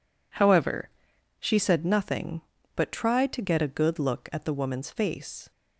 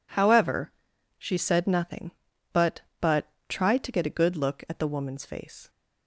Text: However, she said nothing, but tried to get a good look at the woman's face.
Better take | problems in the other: first | says "but" twice; at 2.9 s

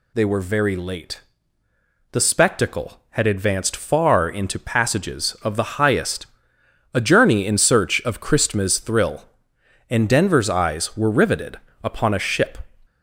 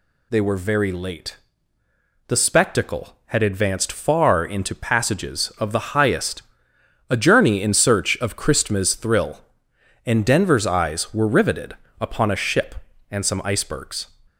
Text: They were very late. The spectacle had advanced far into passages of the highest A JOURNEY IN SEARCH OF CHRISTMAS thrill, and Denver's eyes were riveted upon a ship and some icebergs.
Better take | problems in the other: second | pauses between "highest" and "A"; noticeable; at 6.2 s; 0.70 s long; noticeable in the second // pauses between "riveted" and "upon"; slight; at 11.5 s; 0.26 s long; slight in the second // stops before "and some icebergs"; at 12.8 s

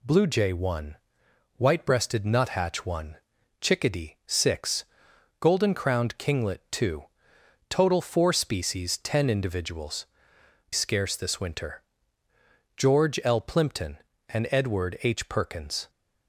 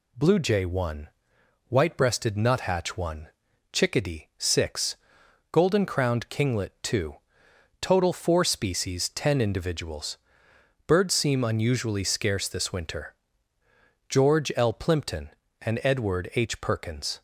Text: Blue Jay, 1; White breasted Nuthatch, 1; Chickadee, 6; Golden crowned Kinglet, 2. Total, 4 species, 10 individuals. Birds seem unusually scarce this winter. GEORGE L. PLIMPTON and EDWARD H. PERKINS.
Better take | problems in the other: second | skips "Birds seem unusually"; at 10.3 s

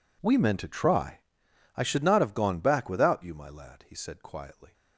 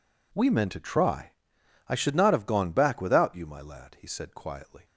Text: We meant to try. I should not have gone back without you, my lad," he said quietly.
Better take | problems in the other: second | gets quieter; strong; throughout; 22 dB

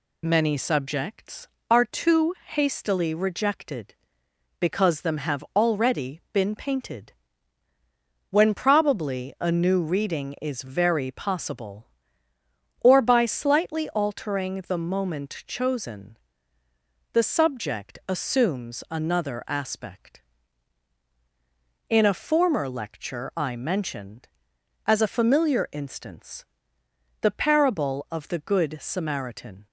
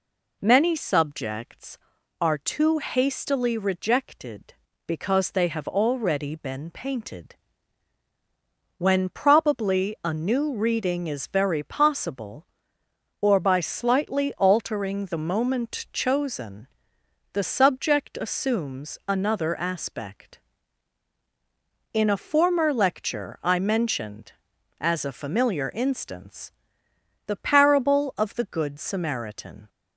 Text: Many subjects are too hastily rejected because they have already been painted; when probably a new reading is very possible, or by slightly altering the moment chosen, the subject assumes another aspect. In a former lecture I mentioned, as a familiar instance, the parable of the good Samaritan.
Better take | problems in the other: second | says "them" for "they"; at 5.0 s

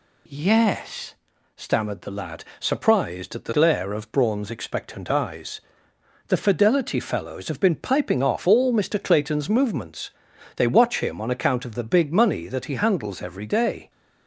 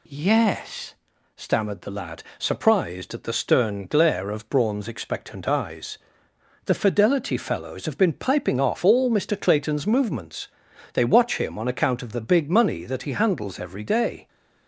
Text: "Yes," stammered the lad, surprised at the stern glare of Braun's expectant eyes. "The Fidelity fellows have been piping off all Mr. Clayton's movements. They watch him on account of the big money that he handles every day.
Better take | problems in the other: second | skips "stern"; at 3.5 s

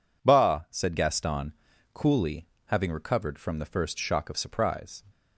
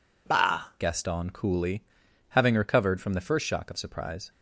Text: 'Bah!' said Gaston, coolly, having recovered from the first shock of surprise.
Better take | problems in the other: first | skips "said"; at 0.7 s

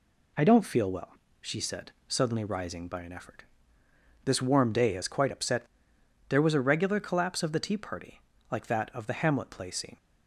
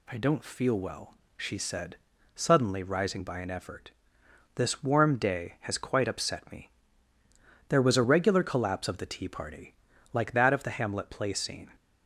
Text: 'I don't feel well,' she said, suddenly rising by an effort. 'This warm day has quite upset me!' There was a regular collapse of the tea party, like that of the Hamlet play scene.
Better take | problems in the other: second | skips "me"; at 5.9 s

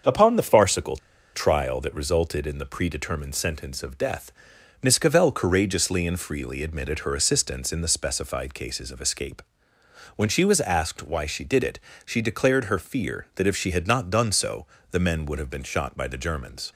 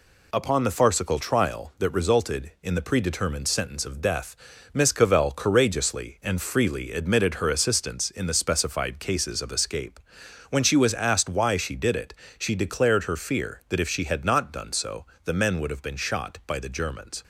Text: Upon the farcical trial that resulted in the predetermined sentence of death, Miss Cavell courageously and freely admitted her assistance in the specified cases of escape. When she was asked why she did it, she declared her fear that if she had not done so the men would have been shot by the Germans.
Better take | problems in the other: second | starts louder than the rest; until 1.4 s; 6.5 dB // pauses between "farcical" and "trial"; at 0.9 s; 0.37 s long // pauses between "so" and "the"; slight; at 14.6 s; 0.26 s long; slight in the second

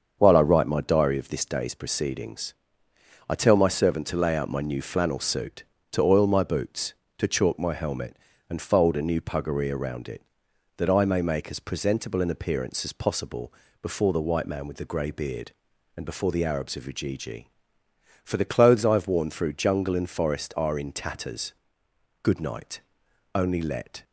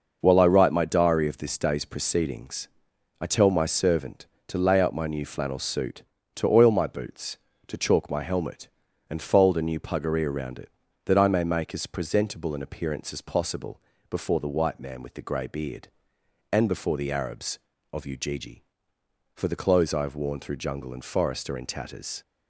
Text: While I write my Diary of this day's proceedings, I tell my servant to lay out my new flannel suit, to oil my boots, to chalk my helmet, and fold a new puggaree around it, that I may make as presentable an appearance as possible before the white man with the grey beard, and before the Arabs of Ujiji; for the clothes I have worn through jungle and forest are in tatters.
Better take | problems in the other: second | starts louder than the rest; until 1.2 s; 7 dB // pauses between "possible" and "before"; slight; at 13.5 s; 0.28 s long; slight in the second // goes on to say "Good night only let"; strong; from 22.2 s on; 1.8 s long

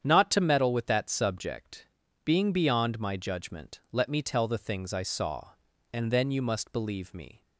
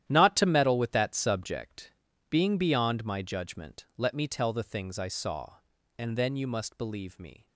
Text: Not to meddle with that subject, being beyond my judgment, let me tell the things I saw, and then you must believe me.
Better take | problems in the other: first | gets quieter; strong; throughout; 12.5 dB // starts louder than the rest; strong; until 1.0 s; 11.5 dB; strong in the first

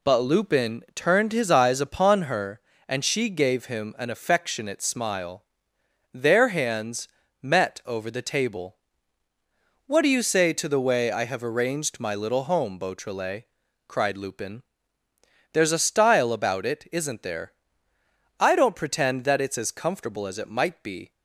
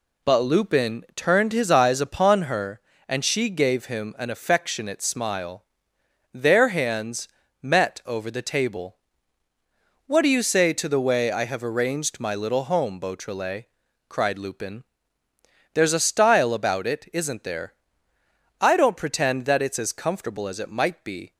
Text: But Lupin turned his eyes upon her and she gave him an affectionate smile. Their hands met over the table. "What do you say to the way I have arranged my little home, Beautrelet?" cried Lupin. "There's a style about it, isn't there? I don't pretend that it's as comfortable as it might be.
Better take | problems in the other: neither | pauses between "hands" and "met"; slight; the same in both

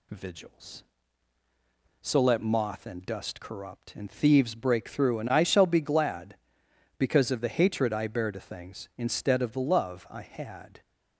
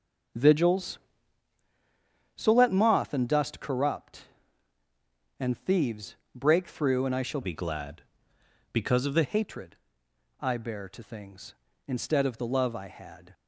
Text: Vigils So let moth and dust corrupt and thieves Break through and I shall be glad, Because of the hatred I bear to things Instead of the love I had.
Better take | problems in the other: first | starts louder than the rest; until 2.7 s; 6.5 dB // pauses between "thieves" and "Break"; slight; at 6.1 s; 0.20 s long // changes voice from "be" to "the"; from 7.4 to 9.2 s; 1.8 s long // pauses between "hatred" and "I"; noticeable; at 9.7 s; 0.64 s long

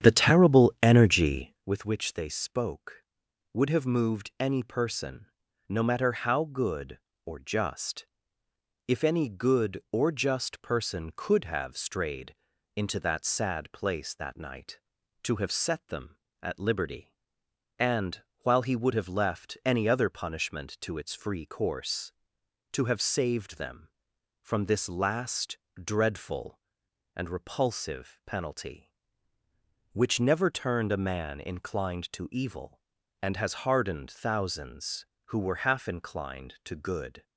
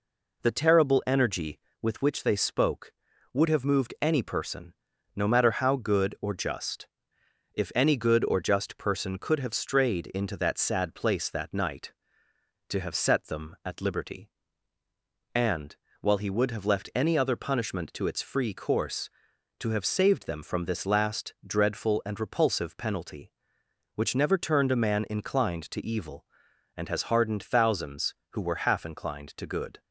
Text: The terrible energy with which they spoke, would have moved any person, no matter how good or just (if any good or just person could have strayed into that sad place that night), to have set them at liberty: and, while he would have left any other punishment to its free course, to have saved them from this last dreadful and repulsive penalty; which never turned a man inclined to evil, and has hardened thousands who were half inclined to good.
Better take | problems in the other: second | starts louder than the rest; strong; until 1.7 s; 9 dB // pauses between "strayed" and "into"; at 12.3 s; 0.41 s long // pauses between "last" and "dreadful"; slight; at 25.5 s; 0.16 s long

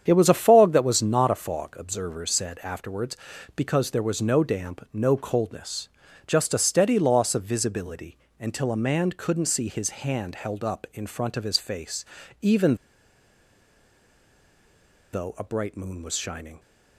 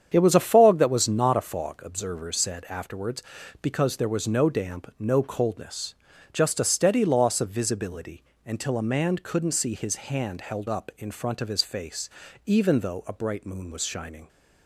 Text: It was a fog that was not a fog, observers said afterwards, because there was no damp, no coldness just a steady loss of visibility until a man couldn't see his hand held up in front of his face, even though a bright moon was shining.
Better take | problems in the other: second | starts louder than the rest; strong; until 1.0 s; 8.5 dB; strong in the second // pauses between "coldness" and "just"; slight; at 5.8 s; 0.36 s long; slight in the second // pauses between "visibility" and "until"; slight; at 8.1 s; 0.24 s long; slight in the second // pauses between "even" and "though"; strong; at 12.7 s; 2.3 s long

